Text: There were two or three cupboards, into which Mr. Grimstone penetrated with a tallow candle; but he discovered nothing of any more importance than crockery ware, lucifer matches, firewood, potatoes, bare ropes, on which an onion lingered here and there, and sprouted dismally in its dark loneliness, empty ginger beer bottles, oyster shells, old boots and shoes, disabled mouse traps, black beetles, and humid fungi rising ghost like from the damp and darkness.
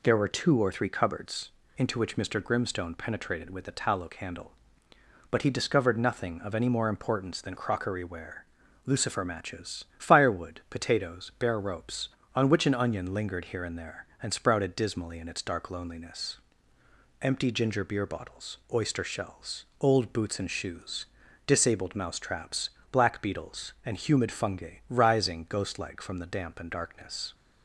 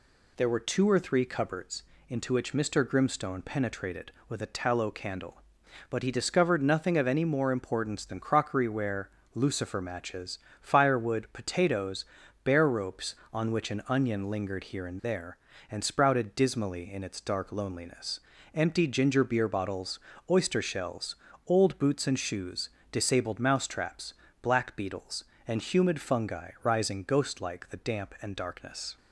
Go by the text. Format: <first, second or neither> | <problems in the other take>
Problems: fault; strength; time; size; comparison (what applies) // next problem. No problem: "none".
first | skips "from"; at 27.7 s